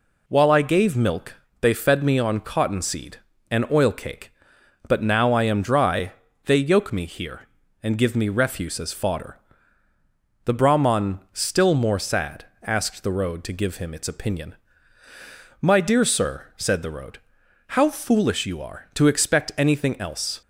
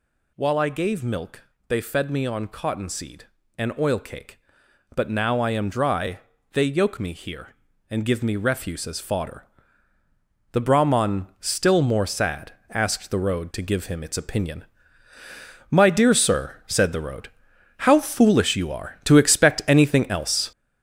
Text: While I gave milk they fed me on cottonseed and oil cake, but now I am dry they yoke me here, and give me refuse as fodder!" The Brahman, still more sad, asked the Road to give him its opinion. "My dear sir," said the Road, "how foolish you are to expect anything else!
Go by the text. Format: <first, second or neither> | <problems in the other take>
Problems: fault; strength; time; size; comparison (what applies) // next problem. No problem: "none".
first | gets louder; throughout; 6.5 dB // pauses between "milk" and "they"; slight; at 1.4 s; 0.26 s long; slight in the first // pauses between "dry" and "they"; slight; at 6.1 s; 0.34 s long; slight in the first